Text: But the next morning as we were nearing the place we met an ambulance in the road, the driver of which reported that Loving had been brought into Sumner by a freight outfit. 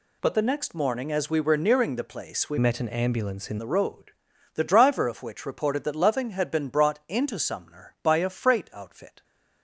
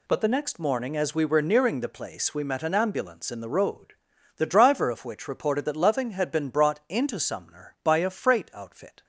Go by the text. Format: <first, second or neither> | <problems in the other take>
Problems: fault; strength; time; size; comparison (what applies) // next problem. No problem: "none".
second | changes voice from "met" to "in"; from 2.5 to 3.5 s; 1.0 s long